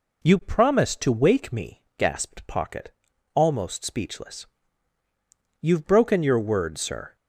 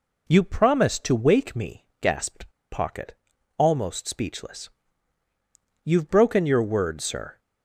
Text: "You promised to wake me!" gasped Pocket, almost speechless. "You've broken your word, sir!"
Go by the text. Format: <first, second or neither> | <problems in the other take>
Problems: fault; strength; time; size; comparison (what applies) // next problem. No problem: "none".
first | pauses between "gasped" and "Pocket"; slight; at 2.5 s; 0.21 s long